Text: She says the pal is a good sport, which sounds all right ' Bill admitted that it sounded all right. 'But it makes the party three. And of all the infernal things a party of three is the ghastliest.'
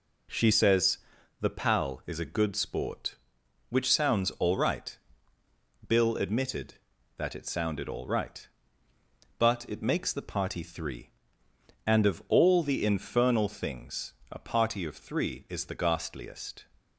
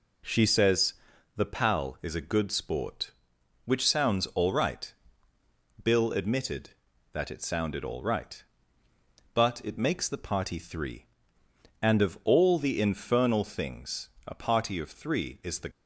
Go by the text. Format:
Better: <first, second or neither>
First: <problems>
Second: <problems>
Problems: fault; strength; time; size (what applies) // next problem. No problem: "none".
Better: first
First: pauses between "says" and "the"; at 0.9 s; 0.42 s long // pauses between "things" and "a"; slight; at 14.1 s; 0.18 s long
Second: pauses between "says" and "the"; at 0.9 s; 0.42 s long // pauses between "things" and "a"; slight; at 14.0 s; 0.18 s long // stops before "ghastliest"; at 15.7 s